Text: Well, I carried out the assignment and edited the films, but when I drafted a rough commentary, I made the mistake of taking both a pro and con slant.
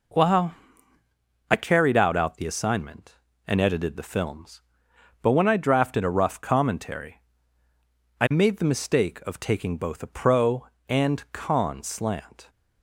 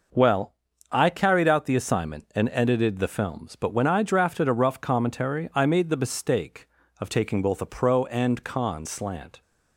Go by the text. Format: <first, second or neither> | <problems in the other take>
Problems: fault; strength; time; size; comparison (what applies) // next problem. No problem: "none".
second | says "out" twice; at 2.1 s